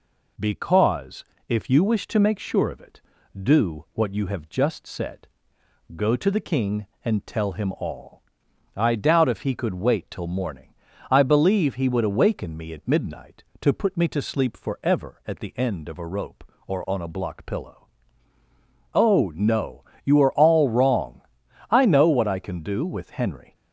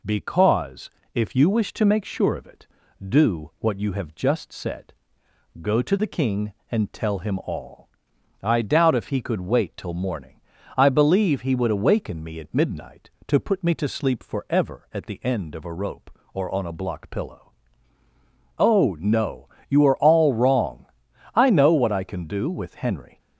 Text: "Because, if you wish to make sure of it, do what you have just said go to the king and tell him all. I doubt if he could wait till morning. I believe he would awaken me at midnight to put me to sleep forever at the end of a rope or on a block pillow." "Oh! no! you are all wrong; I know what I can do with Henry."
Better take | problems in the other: neither | pauses between "said" and "go"; noticeable; the same in both

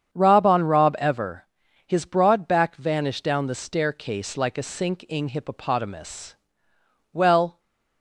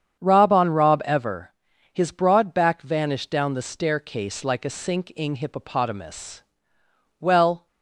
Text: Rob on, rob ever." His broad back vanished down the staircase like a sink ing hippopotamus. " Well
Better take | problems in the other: neither | starts louder than the rest; strong; the same in both

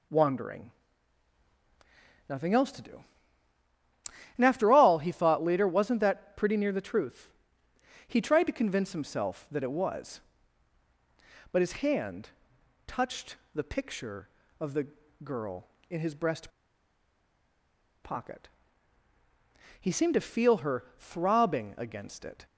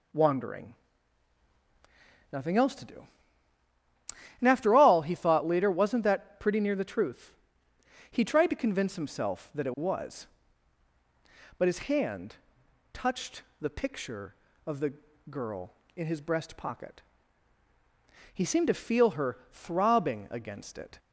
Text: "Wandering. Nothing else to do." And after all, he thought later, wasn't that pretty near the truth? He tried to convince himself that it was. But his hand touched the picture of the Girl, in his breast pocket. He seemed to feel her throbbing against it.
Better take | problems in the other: second | pauses between "hand" and "touched"; noticeable; at 12.3 s; 0.56 s long; noticeable in the second // pauses between "touched" and "the"; slight; at 13.3 s; 0.18 s long; slight in the second // pauses between "the" and "Girl"; at 14.8 s; 0.38 s long; also in the second // pauses between "breast" and "pocket"; strong; at 16.4 s; 1.5 s long

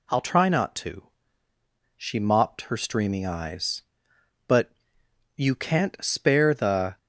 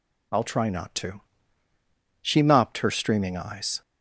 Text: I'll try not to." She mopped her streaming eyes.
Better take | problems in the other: second | goes on to say "But you can't spare the"; strong; from 4.4 s on; 2.5 s long

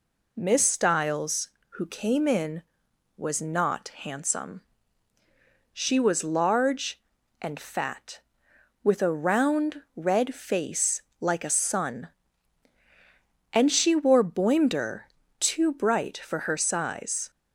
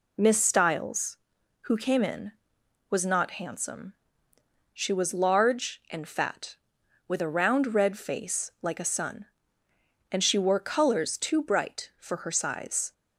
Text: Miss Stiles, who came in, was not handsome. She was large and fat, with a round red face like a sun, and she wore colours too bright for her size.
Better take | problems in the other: second | pauses between "face" and "like"; slight; at 11.0 s; 0.18 s long // says "boimder" for "colours"; at 14.2 s

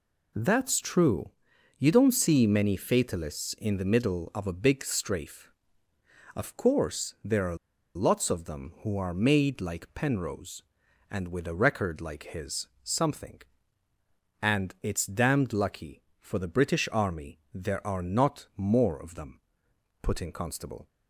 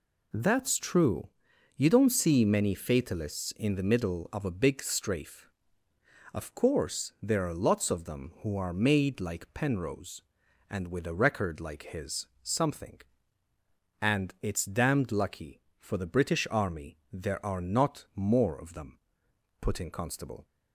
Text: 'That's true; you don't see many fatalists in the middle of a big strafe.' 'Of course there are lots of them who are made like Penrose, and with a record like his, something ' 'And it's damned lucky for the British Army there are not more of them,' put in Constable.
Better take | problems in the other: second | pauses between "are" and "lots"; at 7.5 s; 0.40 s long

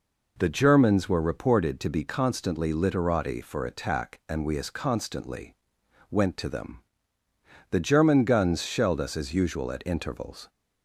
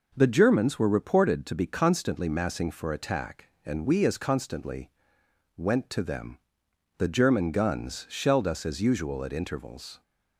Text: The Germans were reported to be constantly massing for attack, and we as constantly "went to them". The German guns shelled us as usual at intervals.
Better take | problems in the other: second | says "literati" for "massing"; at 2.7 s // pauses between "constantly" and "went"; noticeable; at 5.5 s; 0.56 s long; noticeable in the second

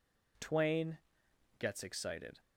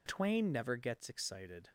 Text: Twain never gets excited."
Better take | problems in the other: second | skips "never"; at 1.2 s

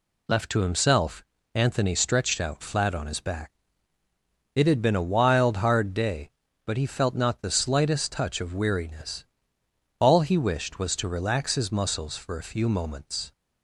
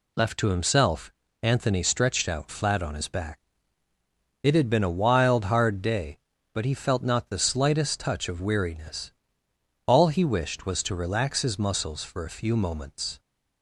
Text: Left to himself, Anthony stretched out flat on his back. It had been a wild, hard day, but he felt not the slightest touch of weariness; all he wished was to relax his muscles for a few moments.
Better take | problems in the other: neither | none

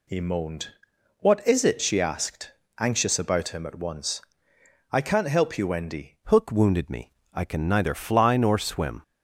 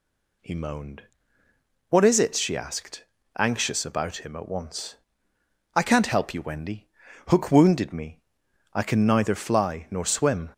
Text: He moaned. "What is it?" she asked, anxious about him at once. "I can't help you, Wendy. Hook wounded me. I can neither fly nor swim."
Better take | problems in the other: second | changes voice at "Hook"; from 6.2 s on; 2.8 s long

